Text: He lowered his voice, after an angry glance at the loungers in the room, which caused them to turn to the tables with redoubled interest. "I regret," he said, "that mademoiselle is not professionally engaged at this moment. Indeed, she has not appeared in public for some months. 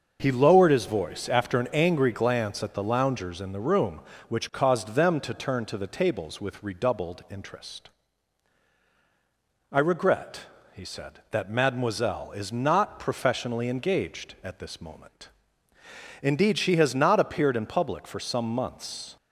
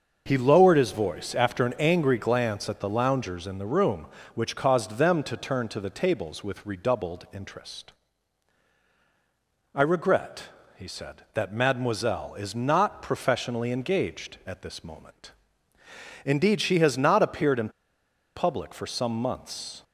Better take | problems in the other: first | starts louder than the rest; until 1.2 s; 6.5 dB; also in the first // pauses between "in" and "public"; noticeable; at 17.6 s; 0.67 s long

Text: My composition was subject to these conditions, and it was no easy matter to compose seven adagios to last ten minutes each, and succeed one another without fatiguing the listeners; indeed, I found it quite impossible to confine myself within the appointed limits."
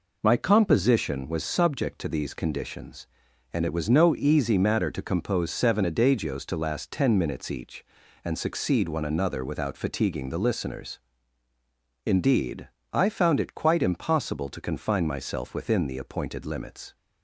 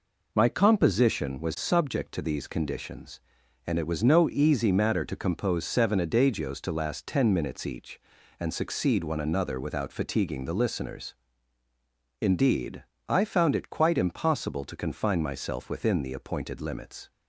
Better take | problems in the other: neither | none

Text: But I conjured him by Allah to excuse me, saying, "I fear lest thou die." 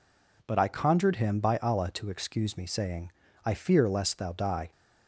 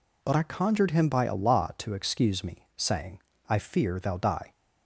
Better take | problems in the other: first | skips "lest"; at 3.9 s

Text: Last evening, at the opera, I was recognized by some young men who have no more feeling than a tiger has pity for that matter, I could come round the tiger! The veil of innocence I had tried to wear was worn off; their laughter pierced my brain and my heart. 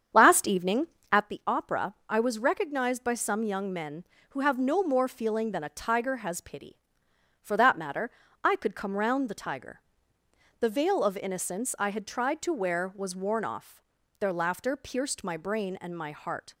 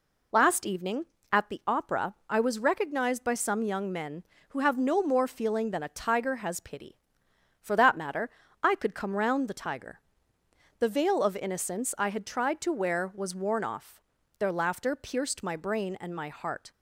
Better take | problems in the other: second | starts louder than the rest; strong; until 1.3 s; 8 dB

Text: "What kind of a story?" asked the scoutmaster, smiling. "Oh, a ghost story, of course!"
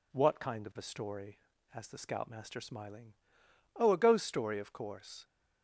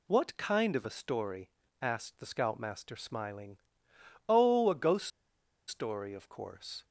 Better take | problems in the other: first | pauses between "ghost" and "story"; noticeable; at 5.0 s; 0.59 s long

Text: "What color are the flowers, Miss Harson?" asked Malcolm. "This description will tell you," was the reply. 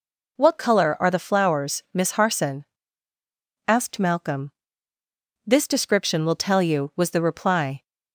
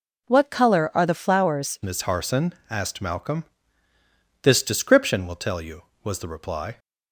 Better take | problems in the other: first | changes voice at "Miss"; from 1.8 s on; 4.9 s long

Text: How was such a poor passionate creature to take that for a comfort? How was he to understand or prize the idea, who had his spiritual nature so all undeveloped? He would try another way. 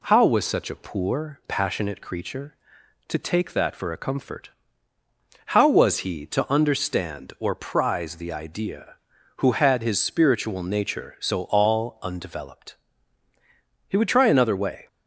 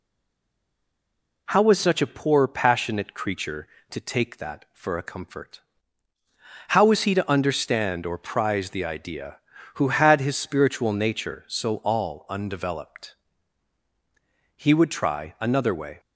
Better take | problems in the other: first | stays silent before the first word; noticeable; until 1.4 s; 1.4 s long

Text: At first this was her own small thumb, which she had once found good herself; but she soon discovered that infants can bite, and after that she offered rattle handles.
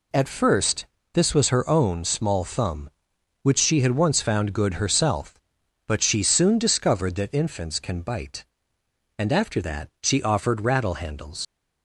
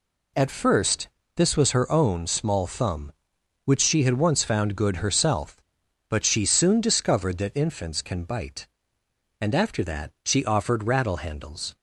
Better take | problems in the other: second | pauses between "first" and "this"; slight; at 0.8 s; 0.28 s long; slight in the second // leaves "handles" unfinished; at 11.4 s; 80 ms

